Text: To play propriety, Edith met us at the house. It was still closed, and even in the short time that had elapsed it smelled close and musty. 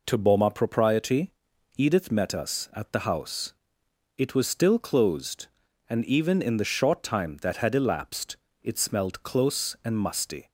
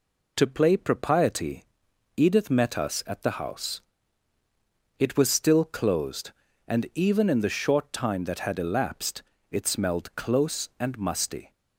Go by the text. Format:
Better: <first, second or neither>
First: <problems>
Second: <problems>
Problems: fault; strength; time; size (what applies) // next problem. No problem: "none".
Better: second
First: says "boma" for "play"; at 0.1 s // pauses between "elapsed" and "it"; slight; at 8.3 s; 0.26 s long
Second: pauses between "elapsed" and "it"; slight; at 9.2 s; 0.28 s long